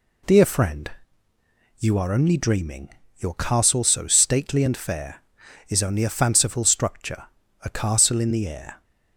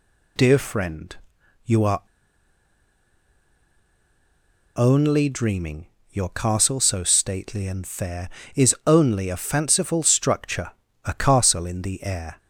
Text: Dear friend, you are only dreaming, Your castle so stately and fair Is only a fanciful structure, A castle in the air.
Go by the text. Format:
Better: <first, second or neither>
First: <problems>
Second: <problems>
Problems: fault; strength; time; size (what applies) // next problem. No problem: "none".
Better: first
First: none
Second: pauses between "are" and "only"; strong; at 2.0 s; 2.7 s long